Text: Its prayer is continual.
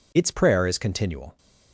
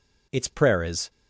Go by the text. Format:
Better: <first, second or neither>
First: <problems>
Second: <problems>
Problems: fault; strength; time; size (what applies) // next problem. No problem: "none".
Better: first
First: none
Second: stops before "continual"; at 1.0 s